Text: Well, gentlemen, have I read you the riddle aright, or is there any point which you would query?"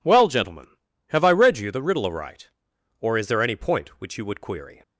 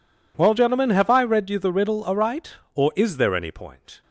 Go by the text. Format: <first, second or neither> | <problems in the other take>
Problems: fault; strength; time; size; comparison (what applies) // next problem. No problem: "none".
first | stops before "which you would query"; at 4.0 s